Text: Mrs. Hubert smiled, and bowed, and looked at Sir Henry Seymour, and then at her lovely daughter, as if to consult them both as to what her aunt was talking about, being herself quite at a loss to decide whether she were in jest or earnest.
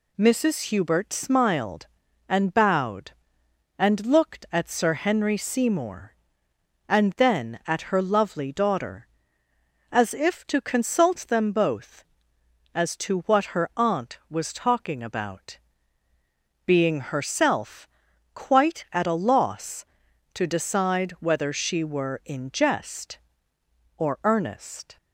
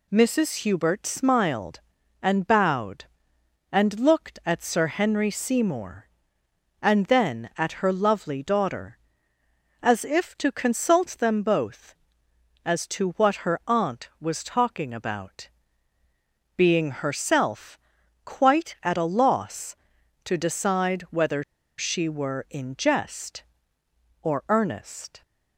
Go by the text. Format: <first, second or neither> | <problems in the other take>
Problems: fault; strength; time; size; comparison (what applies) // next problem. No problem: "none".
first | pauses between "herself" and "quite"; noticeable; at 17.7 s; 0.46 s long; noticeable in the first // pauses between "whether" and "she"; at 21.4 s; 0.36 s long